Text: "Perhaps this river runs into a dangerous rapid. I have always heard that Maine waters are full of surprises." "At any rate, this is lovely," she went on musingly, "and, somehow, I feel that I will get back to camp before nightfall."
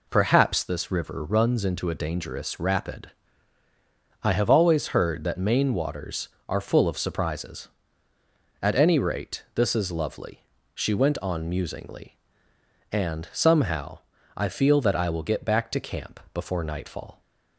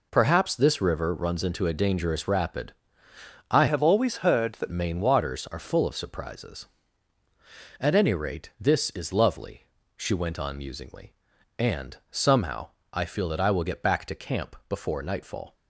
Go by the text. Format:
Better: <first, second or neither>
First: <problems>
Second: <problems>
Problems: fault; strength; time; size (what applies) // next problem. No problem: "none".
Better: first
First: none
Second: changes voice from "have" to "that"; from 3.6 to 4.7 s; 1.1 s long